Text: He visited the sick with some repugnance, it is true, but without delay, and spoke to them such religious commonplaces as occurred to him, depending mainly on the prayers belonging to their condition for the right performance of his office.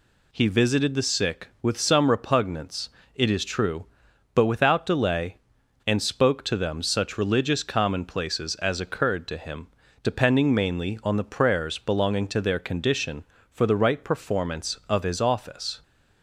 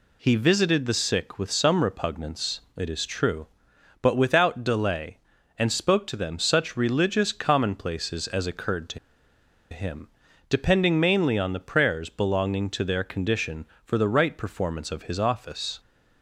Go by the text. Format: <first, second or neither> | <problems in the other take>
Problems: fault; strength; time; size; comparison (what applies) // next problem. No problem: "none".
first | pauses between "to" and "him"; noticeable; at 8.9 s; 0.73 s long